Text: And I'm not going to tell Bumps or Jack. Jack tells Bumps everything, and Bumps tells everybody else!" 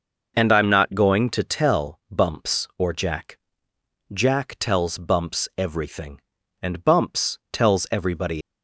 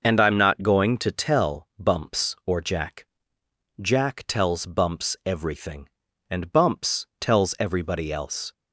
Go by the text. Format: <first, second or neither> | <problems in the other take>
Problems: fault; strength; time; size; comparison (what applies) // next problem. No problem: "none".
second | stops before "else"; at 8.4 s